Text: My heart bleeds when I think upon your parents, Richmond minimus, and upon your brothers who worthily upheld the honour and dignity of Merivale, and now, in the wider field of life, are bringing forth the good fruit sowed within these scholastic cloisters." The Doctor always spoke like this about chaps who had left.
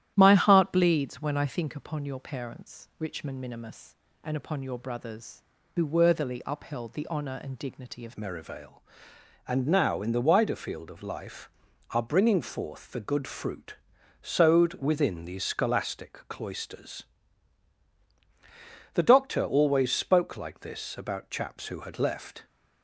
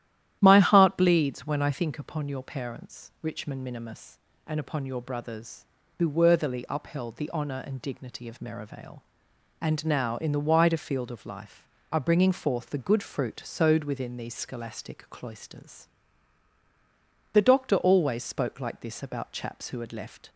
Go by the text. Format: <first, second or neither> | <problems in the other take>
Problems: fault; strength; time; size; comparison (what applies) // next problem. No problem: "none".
second | starts louder than the rest; strong; until 1.1 s; 12 dB; strong in the second // changes voice at "Merivale"; from 8.1 s on; 14.3 s long // pauses between "fruit" and "sowed"; noticeable; at 13.7 s; 0.46 s long